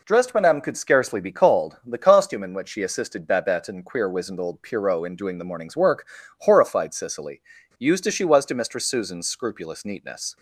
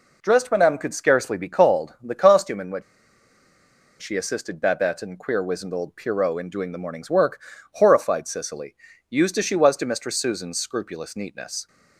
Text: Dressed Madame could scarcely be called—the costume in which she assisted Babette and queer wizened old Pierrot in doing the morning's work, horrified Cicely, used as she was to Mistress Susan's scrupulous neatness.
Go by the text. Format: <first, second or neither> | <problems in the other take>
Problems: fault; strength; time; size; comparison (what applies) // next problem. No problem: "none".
first | pauses between "which" and "she"; at 2.8 s; 1.1 s long